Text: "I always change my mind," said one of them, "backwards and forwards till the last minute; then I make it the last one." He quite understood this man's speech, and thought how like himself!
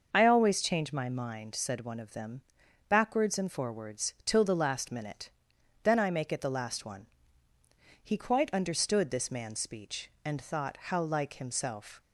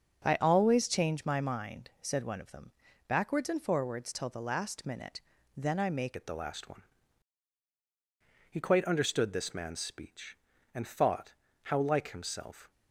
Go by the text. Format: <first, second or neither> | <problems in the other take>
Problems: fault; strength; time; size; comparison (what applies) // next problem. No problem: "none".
first | starts louder than the rest; until 1.2 s; 6.5 dB; noticeable in the first // changes voice at "it"; from 6.1 s on; 6.6 s long // pauses between "thought" and "how"; slight; at 11.3 s; 0.32 s long